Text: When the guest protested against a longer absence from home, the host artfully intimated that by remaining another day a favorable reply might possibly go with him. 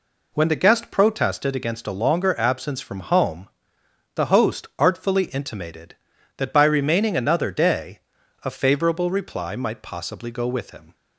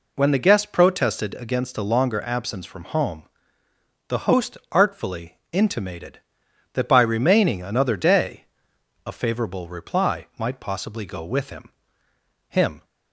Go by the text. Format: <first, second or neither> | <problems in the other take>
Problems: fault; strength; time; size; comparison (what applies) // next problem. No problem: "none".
first | pauses between "day" and "a"; noticeable; at 8.4 s; 0.62 s long; also in the first // says "him" twice; at 12.4 s